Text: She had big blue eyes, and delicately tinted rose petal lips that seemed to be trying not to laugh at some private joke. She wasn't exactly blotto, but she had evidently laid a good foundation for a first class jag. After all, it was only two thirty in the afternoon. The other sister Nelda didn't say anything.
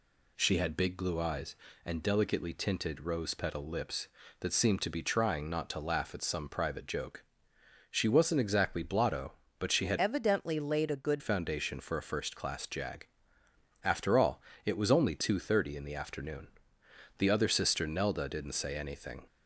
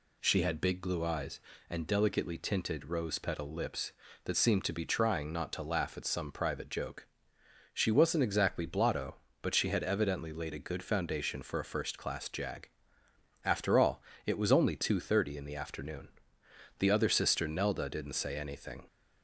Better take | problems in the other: second | changes voice from "evidently" to "good"; from 9.9 to 11.2 s; 1.3 s long

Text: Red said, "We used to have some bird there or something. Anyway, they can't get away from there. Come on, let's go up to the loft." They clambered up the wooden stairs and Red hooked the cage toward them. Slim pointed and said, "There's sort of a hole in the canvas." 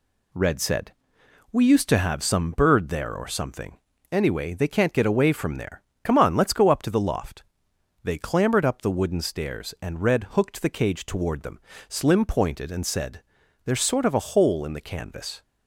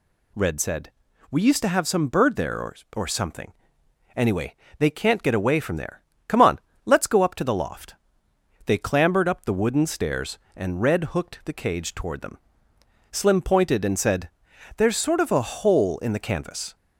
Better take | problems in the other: first | says "or" twice; at 2.9 s

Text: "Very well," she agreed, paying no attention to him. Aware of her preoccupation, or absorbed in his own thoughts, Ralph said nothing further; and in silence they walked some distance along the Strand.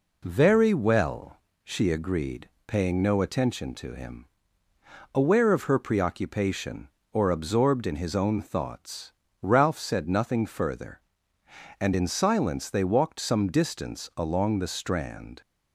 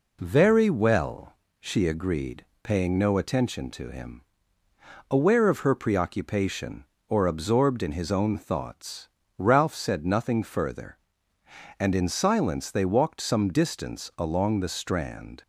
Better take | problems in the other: neither | none

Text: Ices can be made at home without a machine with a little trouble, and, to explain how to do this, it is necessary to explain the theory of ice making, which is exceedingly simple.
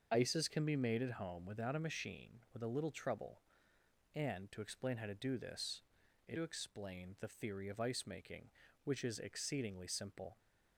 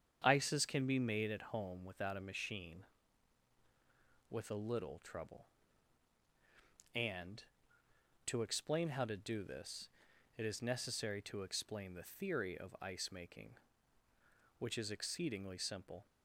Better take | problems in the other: second | starts louder than the rest; until 1.1 s; 6.5 dB; strong in the second // skips "is necessary"; at 6.3 s

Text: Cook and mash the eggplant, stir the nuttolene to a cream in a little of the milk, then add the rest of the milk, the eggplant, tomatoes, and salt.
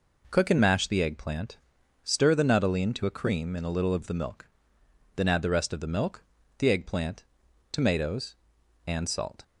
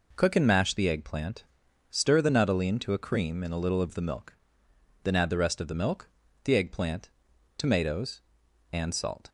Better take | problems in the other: neither | none

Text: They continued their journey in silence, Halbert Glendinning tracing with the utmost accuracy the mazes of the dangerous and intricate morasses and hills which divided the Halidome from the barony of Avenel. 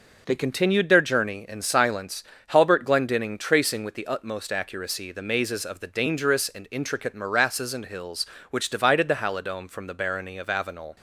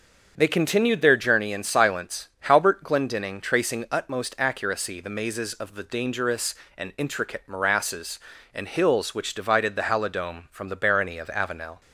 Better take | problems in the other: first | starts louder than the rest; until 1.3 s; 6.5 dB // skips "with the"; at 3.8 s

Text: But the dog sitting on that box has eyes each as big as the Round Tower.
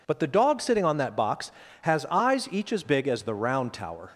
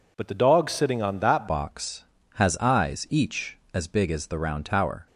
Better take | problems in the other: first | changes voice at "box"; from 1.4 s on; 3.6 s long

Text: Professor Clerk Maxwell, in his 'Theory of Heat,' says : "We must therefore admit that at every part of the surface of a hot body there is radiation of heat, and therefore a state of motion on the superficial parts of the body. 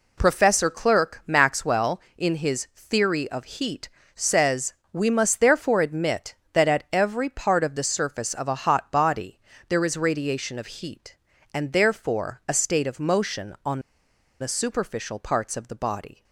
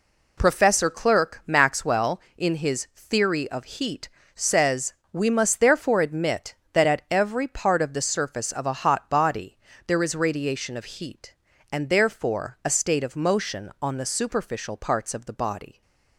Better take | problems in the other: second | pauses between "body" and "there"; slight; at 9.3 s; 0.30 s long; slight in the second // pauses between "on" and "the"; noticeable; at 13.7 s; 0.61 s long

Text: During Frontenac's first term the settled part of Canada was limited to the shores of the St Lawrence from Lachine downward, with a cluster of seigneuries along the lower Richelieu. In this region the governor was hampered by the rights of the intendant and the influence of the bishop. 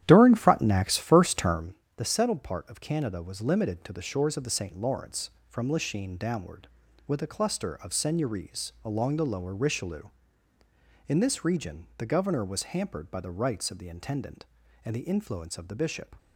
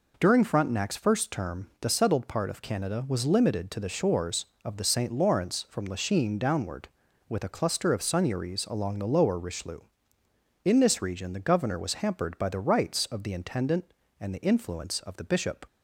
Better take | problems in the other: second | starts louder than the rest; strong; until 1.7 s; 11.5 dB // pauses between "term" and "the"; slight; at 1.7 s; 0.18 s long

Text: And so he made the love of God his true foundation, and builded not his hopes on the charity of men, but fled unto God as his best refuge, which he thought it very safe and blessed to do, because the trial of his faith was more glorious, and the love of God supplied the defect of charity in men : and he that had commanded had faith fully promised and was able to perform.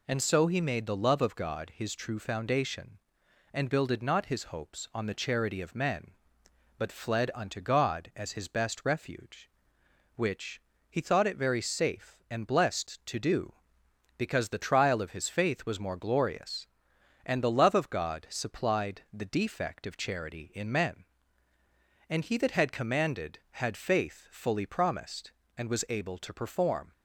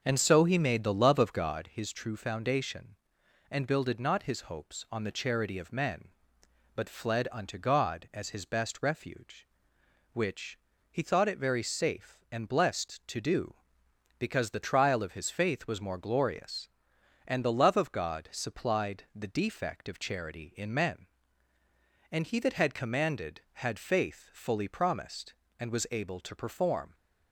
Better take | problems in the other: first | starts louder than the rest; until 1.7 s; 6 dB // pauses between "which" and "he"; slight; at 10.5 s; 0.34 s long; slight in the first

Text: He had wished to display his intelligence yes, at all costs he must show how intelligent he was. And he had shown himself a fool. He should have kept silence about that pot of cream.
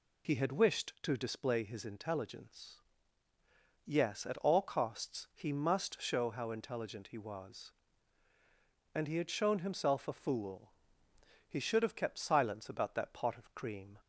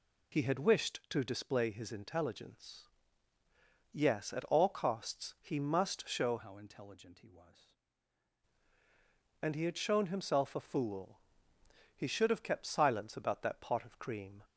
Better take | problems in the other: first | pauses between "intelligence" and "yes"; at 2.8 s; 1.0 s long; also in the first // changes voice from "how" to "was"; from 6.3 to 7.7 s; 1.4 s long

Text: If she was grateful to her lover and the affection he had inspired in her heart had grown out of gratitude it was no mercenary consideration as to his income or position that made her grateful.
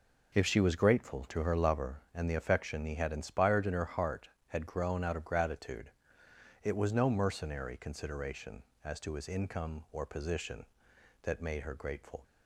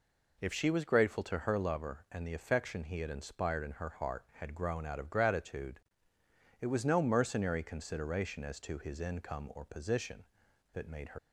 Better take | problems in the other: first | pauses between "gratitude" and "it"; noticeable; at 5.7 s; 0.82 s long; noticeable in the first // stops before "grateful"; at 11.1 s

